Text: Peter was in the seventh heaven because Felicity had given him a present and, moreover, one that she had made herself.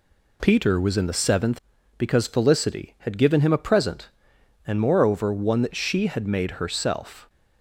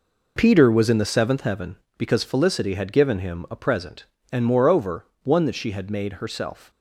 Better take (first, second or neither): second